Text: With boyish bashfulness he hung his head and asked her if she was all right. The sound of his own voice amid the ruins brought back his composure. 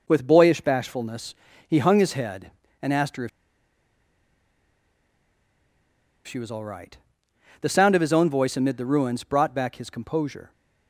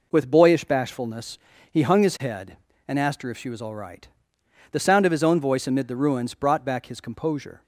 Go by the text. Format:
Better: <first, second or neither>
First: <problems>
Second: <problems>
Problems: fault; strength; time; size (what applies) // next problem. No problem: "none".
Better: second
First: pauses between "bashfulness" and "he"; slight; at 1.3 s; 0.32 s long // pauses between "if" and "she"; strong; at 3.2 s; 2.9 s long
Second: pauses between "bashfulness" and "he"; slight; at 1.3 s; 0.32 s long